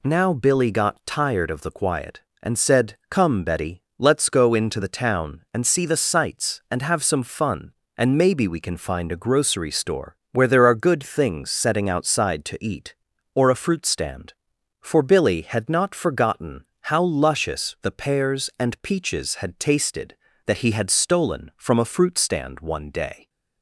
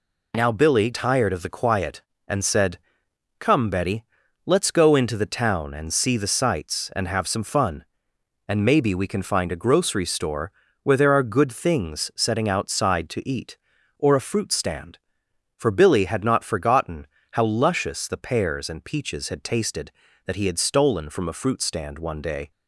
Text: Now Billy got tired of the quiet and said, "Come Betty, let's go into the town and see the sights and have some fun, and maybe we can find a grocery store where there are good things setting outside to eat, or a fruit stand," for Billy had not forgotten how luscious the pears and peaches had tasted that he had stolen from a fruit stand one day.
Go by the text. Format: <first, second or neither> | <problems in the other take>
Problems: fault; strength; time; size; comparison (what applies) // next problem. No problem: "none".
first | skips "got"; at 0.9 s // pauses between "store" and "where"; slight; at 10.5 s; 0.32 s long; slight in the first // pauses between "forgotten" and "how"; slight; at 17.0 s; 0.26 s long; slight in the first